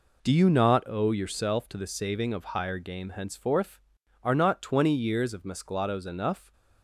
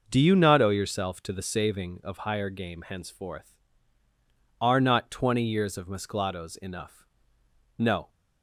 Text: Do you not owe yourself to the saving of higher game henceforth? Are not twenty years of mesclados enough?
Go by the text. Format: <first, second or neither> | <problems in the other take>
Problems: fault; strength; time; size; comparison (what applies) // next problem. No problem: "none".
first | goes on to say "No"; slight; from 7.7 s on; 0.32 s long